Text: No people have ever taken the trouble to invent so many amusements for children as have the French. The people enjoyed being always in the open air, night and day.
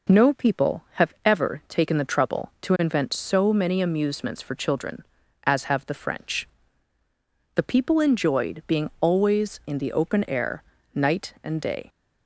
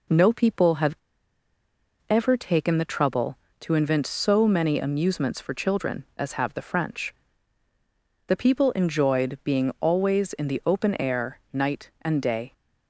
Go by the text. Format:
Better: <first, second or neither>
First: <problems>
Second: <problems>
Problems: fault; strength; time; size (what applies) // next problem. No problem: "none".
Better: first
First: none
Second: pauses between "have" and "ever"; at 0.9 s; 1.1 s long